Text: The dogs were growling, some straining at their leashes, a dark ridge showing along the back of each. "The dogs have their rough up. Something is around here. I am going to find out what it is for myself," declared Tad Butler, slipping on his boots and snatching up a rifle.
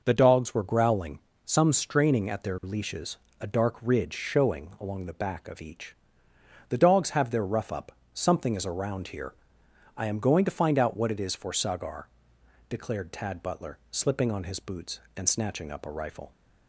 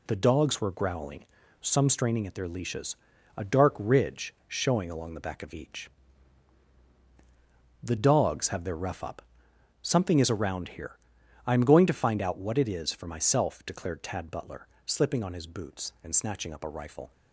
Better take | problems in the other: second | says "sagar" for "myself"; at 11.5 s

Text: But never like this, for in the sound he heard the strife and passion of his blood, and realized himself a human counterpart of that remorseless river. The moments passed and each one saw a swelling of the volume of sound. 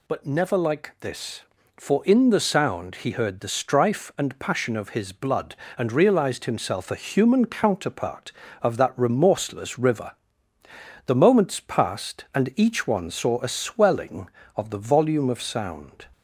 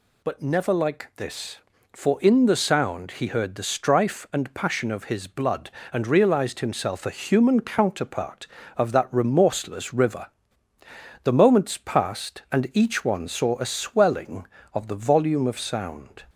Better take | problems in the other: neither | none

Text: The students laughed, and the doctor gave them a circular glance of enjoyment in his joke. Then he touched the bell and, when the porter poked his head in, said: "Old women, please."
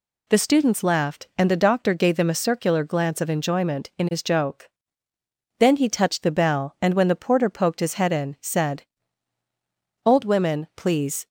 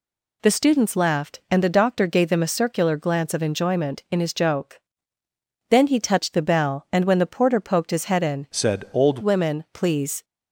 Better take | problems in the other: first | changes voice from "said" to "Old"; from 8.5 to 9.1 s; 0.6 s long

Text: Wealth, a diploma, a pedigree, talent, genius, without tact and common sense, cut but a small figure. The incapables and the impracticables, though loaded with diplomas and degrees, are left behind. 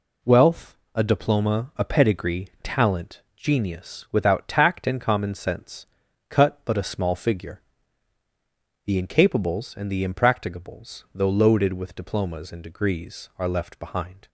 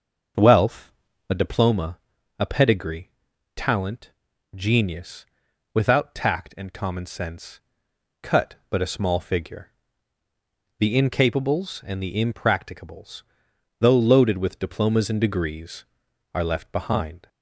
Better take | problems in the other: first | starts louder than the rest; until 1.6 s; 6.5 dB

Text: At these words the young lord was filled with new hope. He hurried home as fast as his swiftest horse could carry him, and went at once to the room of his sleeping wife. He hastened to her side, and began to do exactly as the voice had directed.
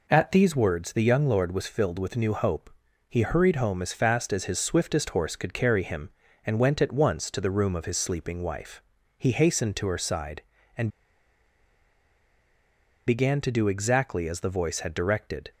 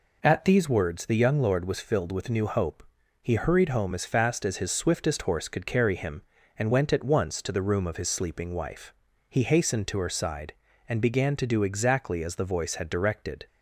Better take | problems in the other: second | pauses between "and" and "began"; strong; at 10.8 s; 2.1 s long

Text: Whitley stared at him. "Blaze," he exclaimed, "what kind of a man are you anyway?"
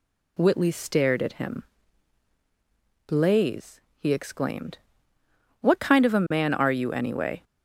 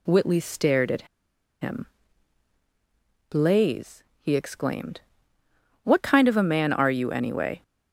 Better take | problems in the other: first | pauses between "at" and "him"; noticeable; at 1.0 s; 0.56 s long

